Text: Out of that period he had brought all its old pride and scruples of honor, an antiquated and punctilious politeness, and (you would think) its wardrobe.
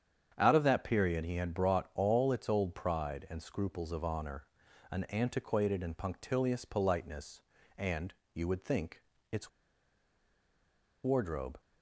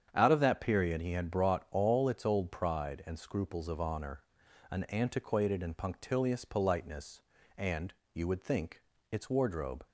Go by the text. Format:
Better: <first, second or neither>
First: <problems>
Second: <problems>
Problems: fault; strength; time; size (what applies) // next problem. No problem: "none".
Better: second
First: starts louder than the rest; strong; until 1.3 s; 8 dB // pauses between "its" and "wardrobe"; strong; at 9.4 s; 1.5 s long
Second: starts louder than the rest; strong; until 1.1 s; 8 dB